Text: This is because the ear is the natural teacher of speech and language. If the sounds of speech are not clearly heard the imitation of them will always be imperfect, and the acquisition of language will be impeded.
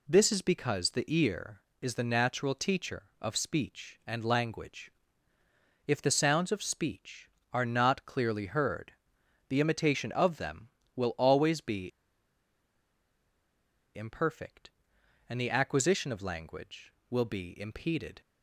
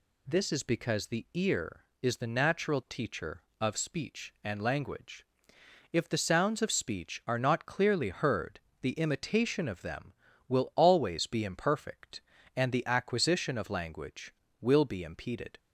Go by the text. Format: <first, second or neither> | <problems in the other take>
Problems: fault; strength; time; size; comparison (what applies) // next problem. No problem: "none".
second | pauses between "heard" and "the"; noticeable; at 8.9 s; 0.56 s long; slight in the second // pauses between "be" and "imperfect"; strong; at 11.9 s; 2.0 s long